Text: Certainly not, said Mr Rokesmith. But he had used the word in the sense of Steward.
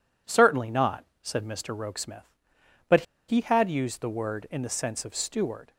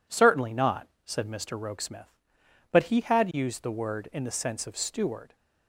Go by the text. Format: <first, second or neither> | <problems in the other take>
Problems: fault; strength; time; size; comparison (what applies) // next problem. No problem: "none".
second | pauses between "But" and "he"; slight; at 3.0 s; 0.26 s long